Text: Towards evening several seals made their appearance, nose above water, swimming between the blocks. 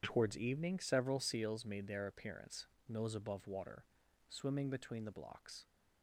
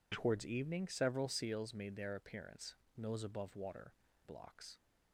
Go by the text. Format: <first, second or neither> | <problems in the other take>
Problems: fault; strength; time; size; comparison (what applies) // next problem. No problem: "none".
first | skips "swimming between the"; at 4.0 s